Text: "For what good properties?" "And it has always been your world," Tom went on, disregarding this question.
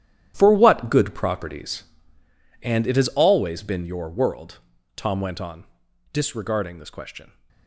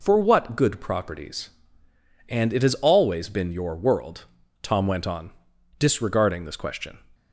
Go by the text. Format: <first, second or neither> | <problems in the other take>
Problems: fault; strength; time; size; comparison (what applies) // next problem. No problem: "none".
second | gets quieter; strong; throughout; 12 dB